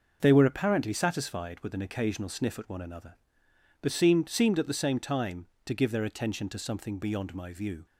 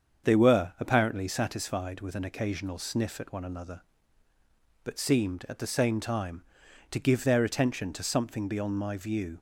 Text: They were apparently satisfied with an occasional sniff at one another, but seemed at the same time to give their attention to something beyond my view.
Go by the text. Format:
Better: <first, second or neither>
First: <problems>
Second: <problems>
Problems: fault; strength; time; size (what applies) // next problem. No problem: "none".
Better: second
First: starts louder than the rest; noticeable; until 1.2 s; 6 dB // says "seemed" twice; at 4.2 s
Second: starts louder than the rest; strong; until 1.3 s; 7 dB